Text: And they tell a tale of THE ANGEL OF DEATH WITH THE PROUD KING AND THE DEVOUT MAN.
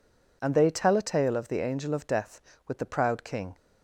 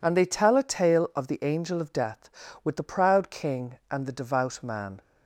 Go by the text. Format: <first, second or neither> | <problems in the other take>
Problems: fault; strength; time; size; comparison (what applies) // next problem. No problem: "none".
second | stops before "AND THE DEVOUT MAN"; at 3.5 s